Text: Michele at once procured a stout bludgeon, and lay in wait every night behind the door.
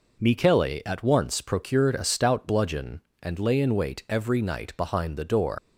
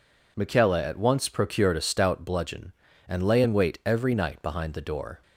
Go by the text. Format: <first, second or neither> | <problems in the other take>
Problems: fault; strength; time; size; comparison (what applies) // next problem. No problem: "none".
second | leaves "door" unfinished; at 5.5 s; 110 ms